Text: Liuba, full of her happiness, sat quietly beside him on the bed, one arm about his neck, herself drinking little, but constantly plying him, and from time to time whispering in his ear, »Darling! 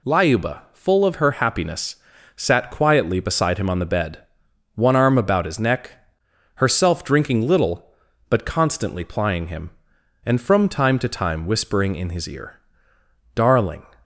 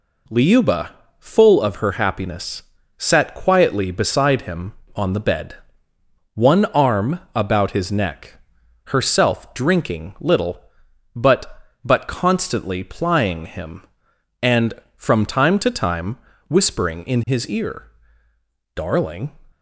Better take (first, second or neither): first